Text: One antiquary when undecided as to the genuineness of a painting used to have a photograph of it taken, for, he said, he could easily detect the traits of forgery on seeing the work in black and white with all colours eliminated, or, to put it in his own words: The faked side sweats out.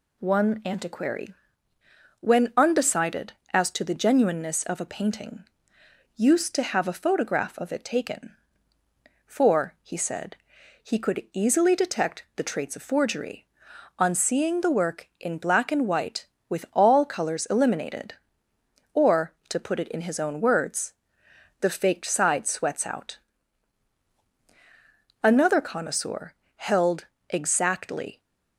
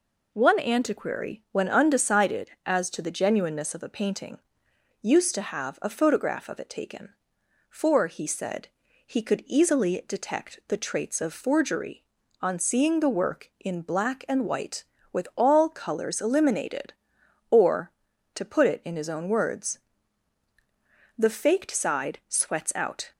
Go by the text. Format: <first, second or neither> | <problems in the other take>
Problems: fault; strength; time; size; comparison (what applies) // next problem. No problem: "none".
second | pauses between "antiquary" and "when"; noticeable; at 1.3 s; 0.88 s long // pauses between "painting" and "used"; noticeable; at 5.4 s; 0.72 s long; noticeable in the second // goes on to say "Another connoisseur held exactly"; strong; from 25.0 s on; 3.1 s long